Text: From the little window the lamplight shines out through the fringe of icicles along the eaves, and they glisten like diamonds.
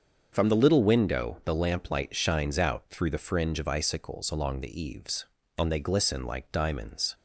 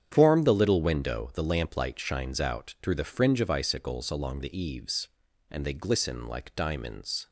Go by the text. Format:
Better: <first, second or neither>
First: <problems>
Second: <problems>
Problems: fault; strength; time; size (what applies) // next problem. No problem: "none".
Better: first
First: starts louder than the rest; until 1.3 s; 7 dB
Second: starts louder than the rest; strong; until 1.1 s; 8.5 dB // says "Form" for "From"; at 0.1 s